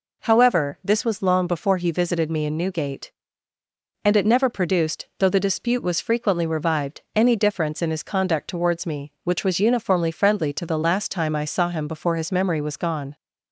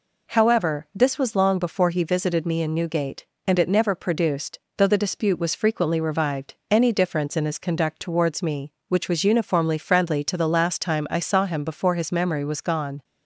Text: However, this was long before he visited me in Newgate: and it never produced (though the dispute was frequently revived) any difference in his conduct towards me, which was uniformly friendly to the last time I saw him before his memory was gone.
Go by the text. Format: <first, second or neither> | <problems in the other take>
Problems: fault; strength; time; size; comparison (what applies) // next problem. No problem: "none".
neither | none